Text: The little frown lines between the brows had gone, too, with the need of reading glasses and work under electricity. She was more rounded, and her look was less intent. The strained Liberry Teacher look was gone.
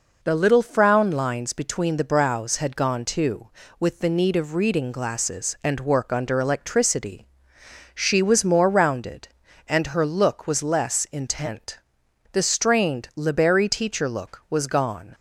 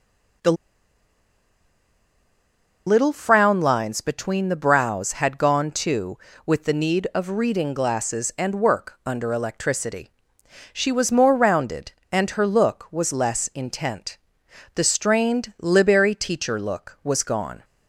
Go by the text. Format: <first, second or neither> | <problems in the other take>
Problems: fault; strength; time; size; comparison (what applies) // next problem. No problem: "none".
first | pauses between "The" and "little"; strong; at 0.5 s; 2.3 s long